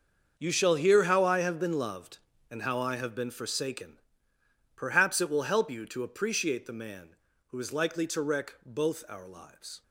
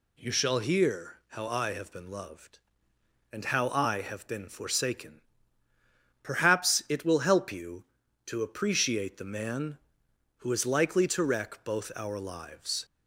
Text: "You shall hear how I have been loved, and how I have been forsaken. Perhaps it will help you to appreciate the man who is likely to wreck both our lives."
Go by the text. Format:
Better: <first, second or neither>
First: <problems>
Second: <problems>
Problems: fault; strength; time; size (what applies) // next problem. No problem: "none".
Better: second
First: gets quieter; strong; throughout; 14 dB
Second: none